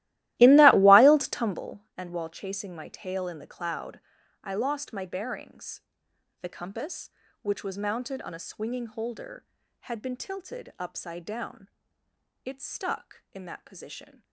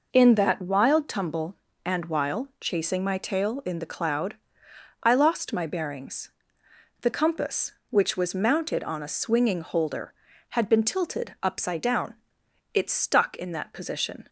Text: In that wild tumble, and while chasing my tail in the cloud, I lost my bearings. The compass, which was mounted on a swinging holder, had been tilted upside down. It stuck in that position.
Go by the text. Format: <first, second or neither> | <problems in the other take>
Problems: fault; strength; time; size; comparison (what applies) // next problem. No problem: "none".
second | starts louder than the rest; strong; until 1.6 s; 16.5 dB